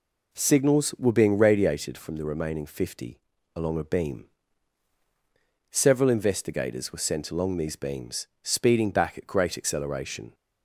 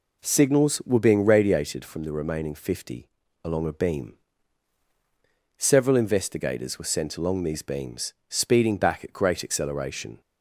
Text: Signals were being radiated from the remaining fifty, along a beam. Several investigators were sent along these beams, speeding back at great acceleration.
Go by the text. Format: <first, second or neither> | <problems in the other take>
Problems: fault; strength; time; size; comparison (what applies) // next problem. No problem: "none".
neither | none